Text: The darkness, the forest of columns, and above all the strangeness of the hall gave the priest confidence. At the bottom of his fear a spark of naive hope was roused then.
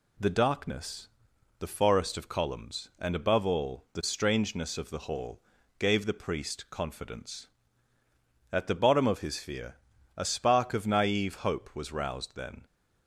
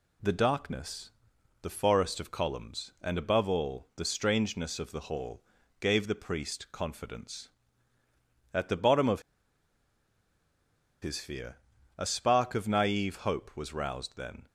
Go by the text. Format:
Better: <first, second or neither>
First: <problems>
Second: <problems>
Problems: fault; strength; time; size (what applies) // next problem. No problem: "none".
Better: first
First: pauses between "hall" and "gave"; at 5.4 s; 0.38 s long // pauses between "fear" and "a"; at 9.7 s; 0.42 s long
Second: pauses between "hall" and "gave"; at 5.4 s; 0.38 s long // pauses between "of" and "his"; strong; at 9.2 s; 1.8 s long // pauses between "fear" and "a"; at 11.5 s; 0.42 s long